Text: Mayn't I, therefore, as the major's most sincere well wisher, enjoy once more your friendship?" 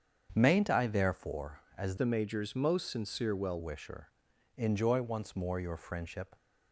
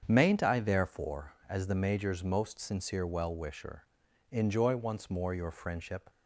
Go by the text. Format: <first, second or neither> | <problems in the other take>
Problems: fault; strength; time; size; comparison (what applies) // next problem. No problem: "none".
second | starts louder than the rest; strong; until 1.3 s; 7.5 dB; strong in the second // changes voice from "the" to "well"; from 1.9 to 3.6 s; 1.7 s long